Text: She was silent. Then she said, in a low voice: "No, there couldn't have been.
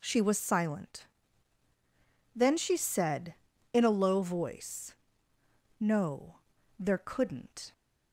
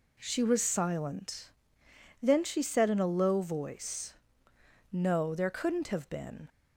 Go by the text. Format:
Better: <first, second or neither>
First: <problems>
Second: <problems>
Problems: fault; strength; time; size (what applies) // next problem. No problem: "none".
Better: second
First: stops before "have been"; at 7.7 s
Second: none